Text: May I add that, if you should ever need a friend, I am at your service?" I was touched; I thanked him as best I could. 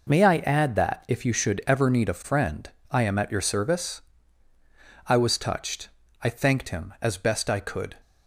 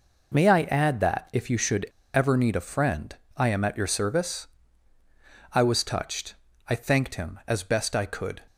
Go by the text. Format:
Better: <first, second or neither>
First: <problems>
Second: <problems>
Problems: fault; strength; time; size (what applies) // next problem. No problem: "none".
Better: first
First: none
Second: pauses between "should" and "ever"; slight; at 1.8 s; 0.29 s long